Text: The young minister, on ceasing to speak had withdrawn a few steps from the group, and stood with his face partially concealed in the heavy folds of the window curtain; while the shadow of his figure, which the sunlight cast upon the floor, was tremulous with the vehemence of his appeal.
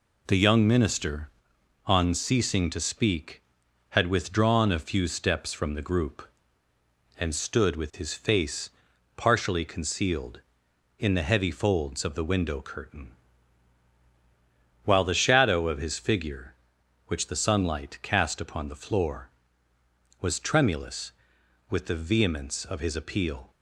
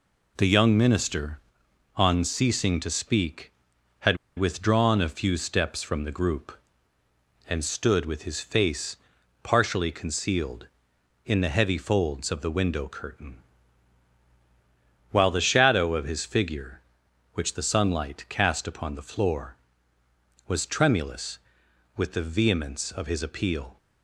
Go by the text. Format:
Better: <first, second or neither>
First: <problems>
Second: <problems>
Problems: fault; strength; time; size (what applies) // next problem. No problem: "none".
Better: first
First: pauses between "face" and "partially"; noticeable; at 8.6 s; 0.48 s long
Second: pauses between "had" and "withdrawn"; slight; at 4.1 s; 0.20 s long // pauses between "face" and "partially"; noticeable; at 8.9 s; 0.48 s long